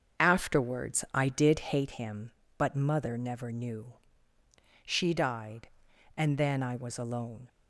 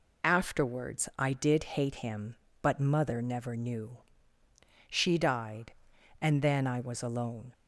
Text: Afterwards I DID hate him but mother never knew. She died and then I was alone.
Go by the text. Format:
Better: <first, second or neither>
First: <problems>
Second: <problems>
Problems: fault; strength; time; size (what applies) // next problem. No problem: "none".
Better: second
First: starts louder than the rest; until 1.9 s; 7 dB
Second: none